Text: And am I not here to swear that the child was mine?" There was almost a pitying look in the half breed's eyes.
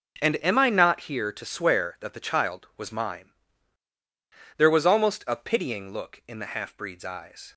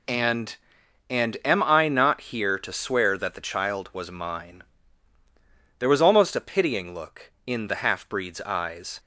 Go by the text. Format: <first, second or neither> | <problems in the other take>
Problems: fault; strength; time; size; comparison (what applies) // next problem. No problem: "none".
first | says "And" twice; at 1.0 s